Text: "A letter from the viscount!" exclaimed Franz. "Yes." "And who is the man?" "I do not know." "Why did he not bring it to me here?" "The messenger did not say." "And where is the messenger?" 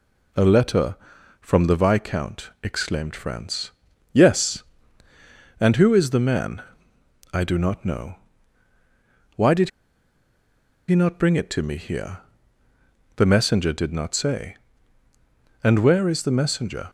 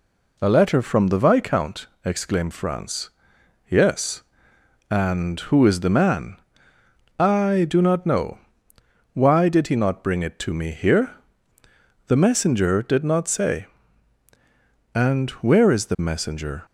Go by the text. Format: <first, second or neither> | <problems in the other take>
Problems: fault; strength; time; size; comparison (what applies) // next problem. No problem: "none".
second | pauses between "did" and "he"; at 9.6 s; 1.1 s long